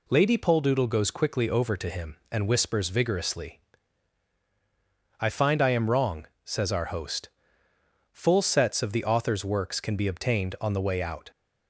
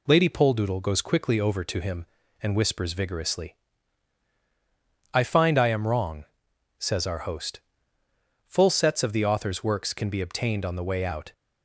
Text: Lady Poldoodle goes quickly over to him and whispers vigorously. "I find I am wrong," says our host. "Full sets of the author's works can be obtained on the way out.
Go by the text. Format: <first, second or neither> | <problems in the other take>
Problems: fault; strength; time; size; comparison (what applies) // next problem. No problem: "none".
neither | none